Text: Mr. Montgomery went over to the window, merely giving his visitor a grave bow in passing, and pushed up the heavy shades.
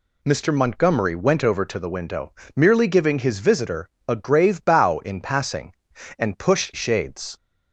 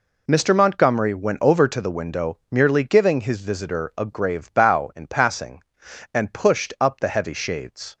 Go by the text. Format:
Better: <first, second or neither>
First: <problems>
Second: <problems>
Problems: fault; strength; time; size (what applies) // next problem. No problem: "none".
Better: second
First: pauses between "visitor" and "a"; slight; at 3.8 s; 0.18 s long // skips "up the heavy"; at 6.7 s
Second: none